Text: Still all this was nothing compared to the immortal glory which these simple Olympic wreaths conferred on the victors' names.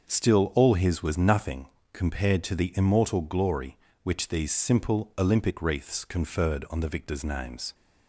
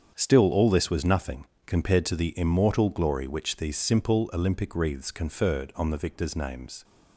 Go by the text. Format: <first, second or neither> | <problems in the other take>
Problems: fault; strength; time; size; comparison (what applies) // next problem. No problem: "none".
second | starts louder than the rest; until 1.1 s; 6.5 dB; strong in the second // says "his" for "this"; at 0.7 s // pauses between "nothing" and "compared"; slight; at 1.6 s; 0.26 s long; slight in the second